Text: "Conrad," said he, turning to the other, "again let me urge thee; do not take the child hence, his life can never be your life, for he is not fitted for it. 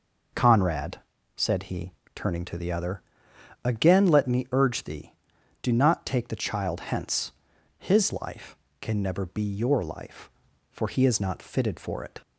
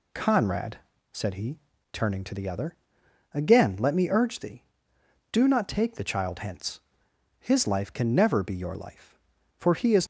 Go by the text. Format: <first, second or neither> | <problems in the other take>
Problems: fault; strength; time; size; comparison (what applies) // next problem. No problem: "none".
first | stops before "not fitted for it"; at 10.0 s